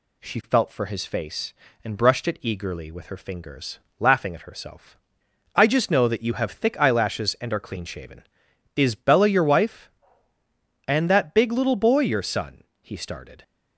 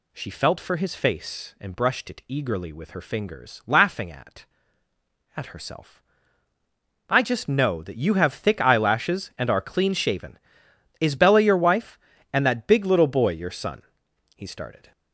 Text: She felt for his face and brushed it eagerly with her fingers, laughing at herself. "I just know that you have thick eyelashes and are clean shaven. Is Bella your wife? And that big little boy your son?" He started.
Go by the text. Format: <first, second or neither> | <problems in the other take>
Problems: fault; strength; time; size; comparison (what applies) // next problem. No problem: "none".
first | says "at" twice; at 5.3 s